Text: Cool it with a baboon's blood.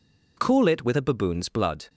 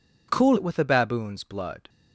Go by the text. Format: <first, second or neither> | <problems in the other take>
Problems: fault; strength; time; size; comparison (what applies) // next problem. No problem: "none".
first | changes voice at "it"; from 0.5 s on; 1.3 s long